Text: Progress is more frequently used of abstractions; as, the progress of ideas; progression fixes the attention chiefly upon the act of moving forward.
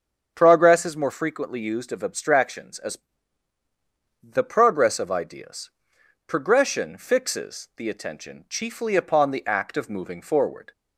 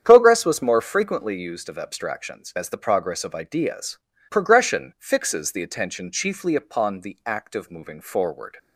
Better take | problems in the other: first | starts louder than the rest; strong; until 1.0 s; 8.5 dB; also in the first // says "was" for "is"; at 0.4 s

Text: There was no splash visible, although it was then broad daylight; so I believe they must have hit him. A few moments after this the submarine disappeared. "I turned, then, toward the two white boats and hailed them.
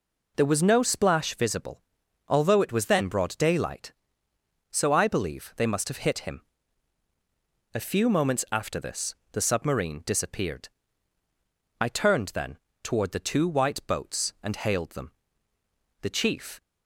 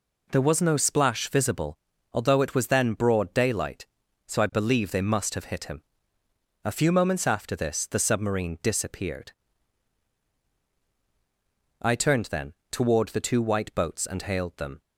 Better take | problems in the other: second | pauses between "this" and "the"; slight; at 9.1 s; 0.16 s long // goes on to say "The chief"; from 16.0 s on; 0.60 s long

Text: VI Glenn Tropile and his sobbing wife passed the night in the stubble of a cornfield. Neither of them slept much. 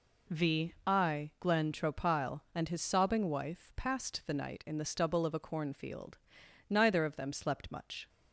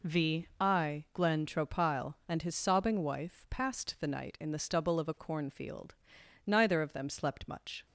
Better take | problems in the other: neither | none

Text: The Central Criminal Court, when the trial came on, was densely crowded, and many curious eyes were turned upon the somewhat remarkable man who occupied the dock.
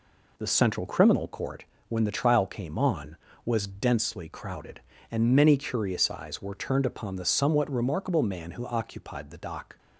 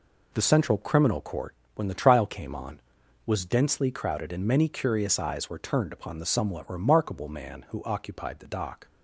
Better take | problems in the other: neither | none

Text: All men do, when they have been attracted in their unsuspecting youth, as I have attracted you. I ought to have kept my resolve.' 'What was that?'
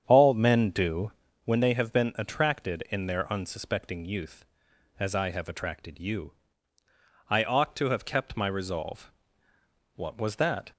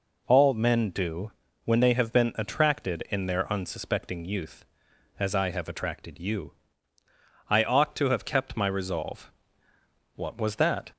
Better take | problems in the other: second | starts louder than the rest; strong; until 1.5 s; 8 dB

